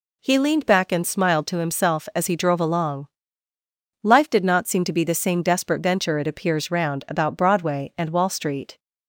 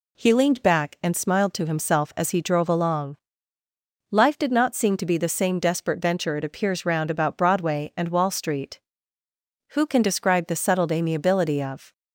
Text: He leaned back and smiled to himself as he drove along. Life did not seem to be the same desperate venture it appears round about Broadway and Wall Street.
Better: first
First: none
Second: goes on to say "Who can describe the settled amiability of"; strong; from 9.7 s on; 2.2 s long

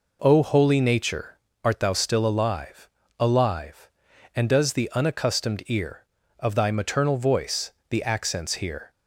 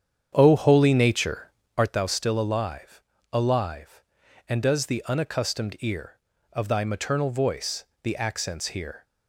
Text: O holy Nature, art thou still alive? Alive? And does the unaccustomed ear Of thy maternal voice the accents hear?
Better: first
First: pauses between "voice" and "the"; slight; at 7.7 s; 0.16 s long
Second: starts louder than the rest; strong; until 2.0 s; 8.5 dB // pauses between "voice" and "the"; slight; at 7.8 s; 0.16 s long

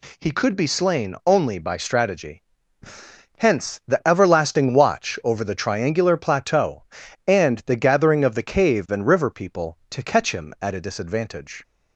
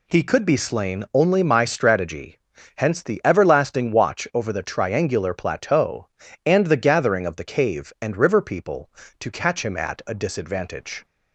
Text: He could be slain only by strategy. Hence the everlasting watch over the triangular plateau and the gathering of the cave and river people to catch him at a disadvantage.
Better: first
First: none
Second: says "my" for "by"; at 1.4 s

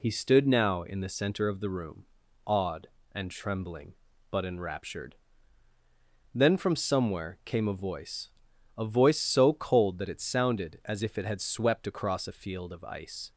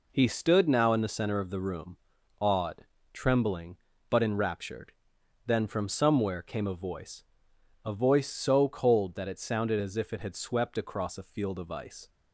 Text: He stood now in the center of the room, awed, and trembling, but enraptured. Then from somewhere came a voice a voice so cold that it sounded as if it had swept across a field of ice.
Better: first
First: pauses between "voice" and "a"; noticeable; at 8.3 s; 0.46 s long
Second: skips "and"; at 2.9 s // pauses between "voice" and "a"; noticeable; at 7.2 s; 0.62 s long

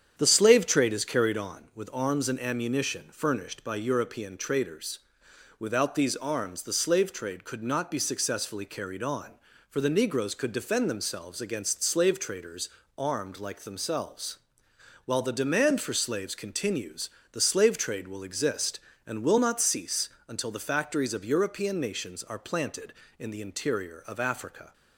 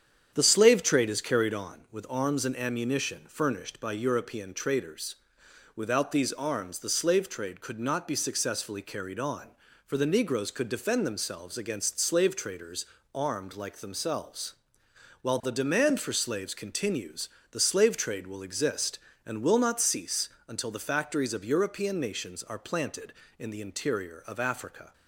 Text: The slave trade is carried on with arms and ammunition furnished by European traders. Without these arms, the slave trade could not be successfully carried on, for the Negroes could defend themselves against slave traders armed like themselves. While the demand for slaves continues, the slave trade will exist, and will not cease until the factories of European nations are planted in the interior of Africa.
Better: neither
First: starts louder than the rest; strong; until 1.1 s; 8.5 dB // pauses between "traders" and "armed"; slight; at 12.6 s; 0.30 s long // pauses between "cease" and "until"; slight; at 20.0 s; 0.18 s long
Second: starts louder than the rest; strong; until 1.3 s; 8.5 dB // pauses between "traders" and "armed"; slight; at 12.8 s; 0.30 s long // pauses between "cease" and "until"; slight; at 20.2 s; 0.18 s long

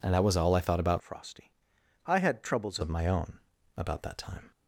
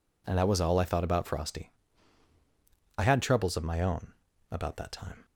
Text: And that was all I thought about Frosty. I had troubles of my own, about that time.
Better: second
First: changes voice from "Frosty" to "troubles"; from 1.0 to 2.7 s; 1.7 s long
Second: none

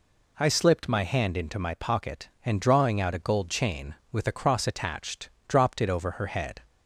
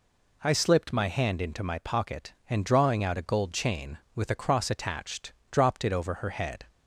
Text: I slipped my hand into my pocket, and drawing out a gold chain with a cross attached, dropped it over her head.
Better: neither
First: none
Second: none

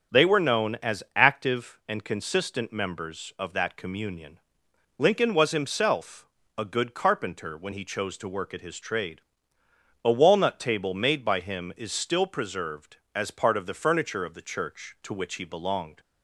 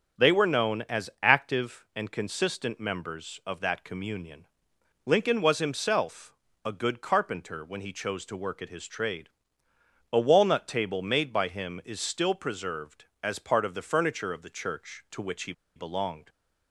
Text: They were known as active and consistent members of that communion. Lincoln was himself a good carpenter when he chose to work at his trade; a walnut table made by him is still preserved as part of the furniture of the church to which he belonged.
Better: first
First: starts louder than the rest; until 1.2 s; 6.5 dB // pauses between "himself" and "a"; slight; at 6.2 s; 0.30 s long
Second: starts louder than the rest; until 1.3 s; 6.5 dB // pauses between "himself" and "a"; slight; at 6.3 s; 0.30 s long // pauses between "he" and "belonged"; slight; at 15.5 s; 0.23 s long

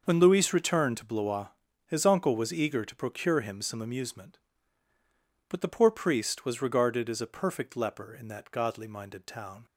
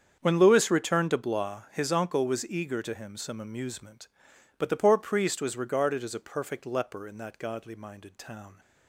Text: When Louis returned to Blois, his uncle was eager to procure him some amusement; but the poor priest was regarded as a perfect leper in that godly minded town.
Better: first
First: starts louder than the rest; noticeable; until 1.0 s; 6 dB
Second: starts louder than the rest; strong; until 1.2 s; 7.5 dB // skips "procure"; at 2.9 s

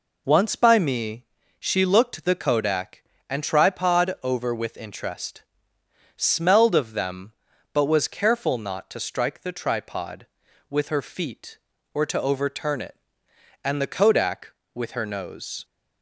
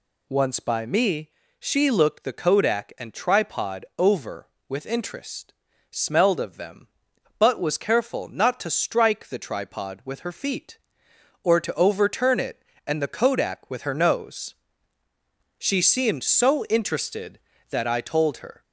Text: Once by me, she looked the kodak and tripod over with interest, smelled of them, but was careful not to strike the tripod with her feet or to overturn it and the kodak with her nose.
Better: first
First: none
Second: goes on to say "She seemed so interested that I told her"; strong; from 15.5 s on; 3.0 s long

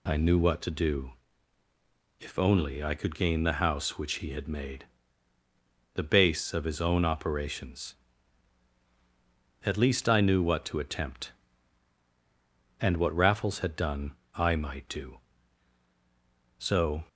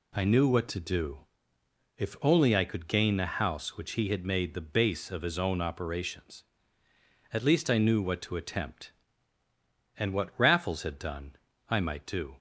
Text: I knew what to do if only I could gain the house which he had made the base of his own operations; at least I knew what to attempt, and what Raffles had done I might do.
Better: second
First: pauses between "do" and "if"; at 1.1 s; 1.1 s long // pauses between "made" and "the"; at 4.8 s; 1.1 s long // pauses between "done" and "I"; slight; at 14.1 s; 0.24 s long // goes on to say "So"; slight; from 16.5 s on; 0.46 s long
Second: pauses between "do" and "if"; noticeable; at 1.2 s; 0.72 s long // pauses between "done" and "I"; slight; at 11.3 s; 0.34 s long

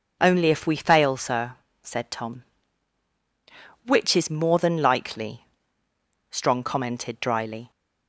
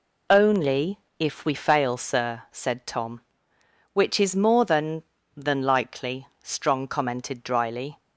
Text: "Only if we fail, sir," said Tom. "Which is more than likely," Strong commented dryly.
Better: first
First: none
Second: pauses between "Only" and "if"; slight; at 0.9 s; 0.22 s long // says "than" twice; at 5.3 s

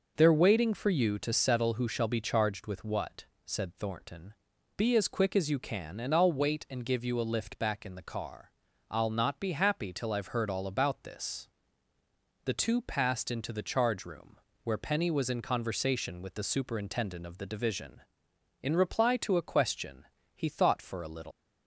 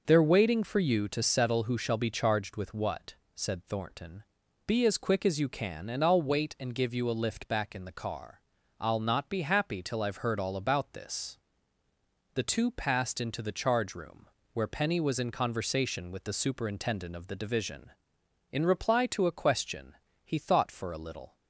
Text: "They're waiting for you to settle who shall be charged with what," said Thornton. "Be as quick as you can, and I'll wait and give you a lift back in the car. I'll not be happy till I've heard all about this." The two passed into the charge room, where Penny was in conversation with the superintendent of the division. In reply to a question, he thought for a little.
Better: second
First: leaves "little" unfinished; at 21.3 s; 145 ms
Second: none

